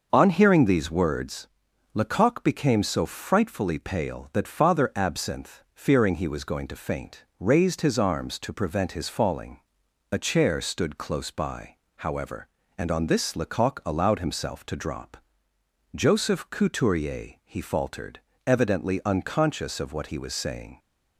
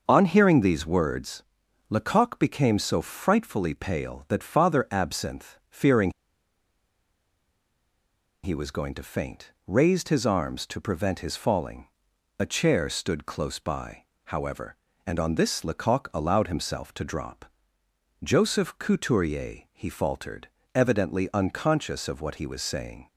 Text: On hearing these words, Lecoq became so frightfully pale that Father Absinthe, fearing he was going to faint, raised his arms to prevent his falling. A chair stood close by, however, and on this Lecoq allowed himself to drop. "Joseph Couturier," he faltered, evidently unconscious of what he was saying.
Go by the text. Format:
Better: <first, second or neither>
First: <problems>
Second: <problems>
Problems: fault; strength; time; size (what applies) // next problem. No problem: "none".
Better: first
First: starts louder than the rest; until 1.1 s; 6 dB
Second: starts louder than the rest; until 1.0 s; 6 dB // pauses between "fearing" and "he"; strong; at 6.1 s; 2.3 s long